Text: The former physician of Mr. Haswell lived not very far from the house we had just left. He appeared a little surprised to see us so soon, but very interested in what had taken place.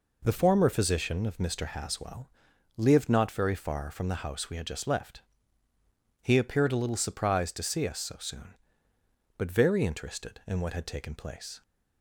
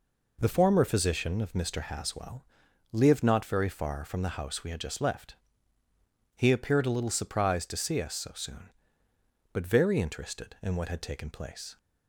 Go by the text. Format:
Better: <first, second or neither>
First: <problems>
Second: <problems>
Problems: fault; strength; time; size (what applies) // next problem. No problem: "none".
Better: neither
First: pauses between "Haswell" and "lived"; noticeable; at 2.2 s; 0.48 s long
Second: pauses between "Haswell" and "lived"; noticeable; at 2.4 s; 0.48 s long